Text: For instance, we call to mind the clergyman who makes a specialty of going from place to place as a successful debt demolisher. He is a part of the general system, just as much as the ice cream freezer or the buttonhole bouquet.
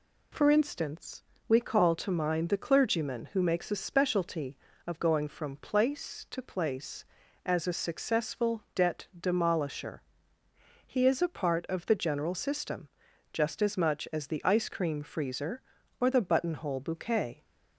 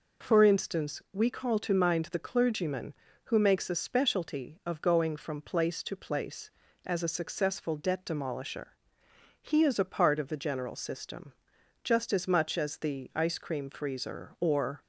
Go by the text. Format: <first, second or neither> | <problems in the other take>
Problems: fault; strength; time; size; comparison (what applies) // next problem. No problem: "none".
first | stops before "the buttonhole bouquet"; at 14.8 s